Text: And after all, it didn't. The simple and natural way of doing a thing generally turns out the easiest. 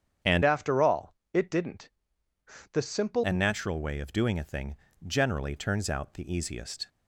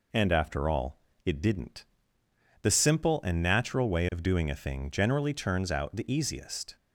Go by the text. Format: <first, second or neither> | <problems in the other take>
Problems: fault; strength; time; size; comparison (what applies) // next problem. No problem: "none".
second | starts louder than the rest; strong; until 1.4 s; 8.5 dB // changes voice from "after" to "simple"; from 0.4 to 3.2 s; 2.8 s long // pauses between "thing" and "generally"; slight; at 4.7 s; 0.30 s long